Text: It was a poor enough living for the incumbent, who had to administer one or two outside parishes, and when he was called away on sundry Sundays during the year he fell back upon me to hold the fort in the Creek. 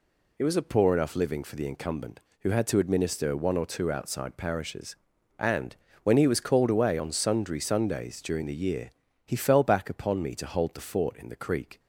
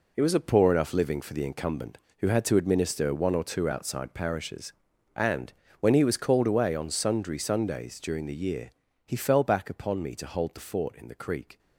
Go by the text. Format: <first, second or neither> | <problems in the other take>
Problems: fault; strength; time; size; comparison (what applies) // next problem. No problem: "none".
first | gets quieter; strong; throughout; 9 dB // pauses between "and" and "when"; slight; at 5.5 s; 0.28 s long; slight in the first // pauses between "year" and "he"; slight; at 8.7 s; 0.34 s long; slight in the first